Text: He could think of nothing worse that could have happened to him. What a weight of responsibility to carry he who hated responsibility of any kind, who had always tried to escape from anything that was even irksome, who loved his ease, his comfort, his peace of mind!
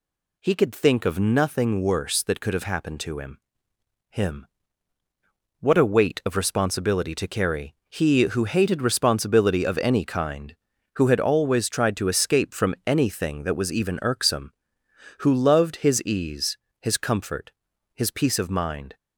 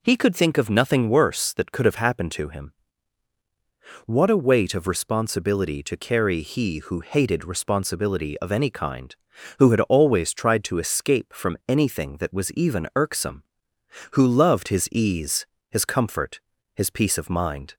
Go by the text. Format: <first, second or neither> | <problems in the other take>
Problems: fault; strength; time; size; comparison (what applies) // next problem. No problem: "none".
second | says "him" twice; at 4.0 s // pauses between "carry" and "he"; slight; at 7.7 s; 0.16 s long